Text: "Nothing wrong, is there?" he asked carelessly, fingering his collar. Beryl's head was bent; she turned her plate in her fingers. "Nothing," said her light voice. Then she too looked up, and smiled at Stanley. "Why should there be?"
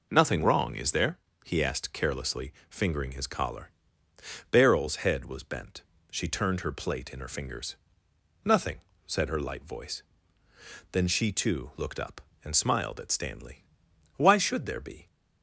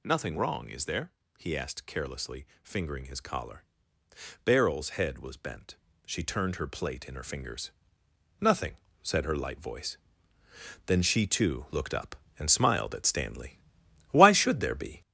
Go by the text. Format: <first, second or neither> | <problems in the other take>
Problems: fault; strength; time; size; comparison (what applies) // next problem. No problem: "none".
first | gets louder; noticeable; throughout; 5 dB